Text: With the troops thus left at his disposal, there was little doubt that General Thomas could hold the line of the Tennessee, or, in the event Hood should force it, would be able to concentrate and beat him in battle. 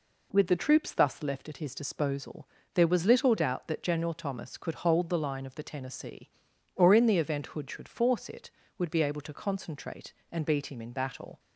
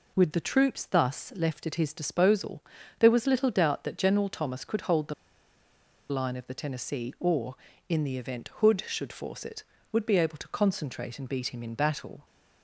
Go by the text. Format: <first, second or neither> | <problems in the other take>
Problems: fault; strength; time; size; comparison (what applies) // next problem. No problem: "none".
first | pauses between "the" and "line"; noticeable; at 5.1 s; 0.97 s long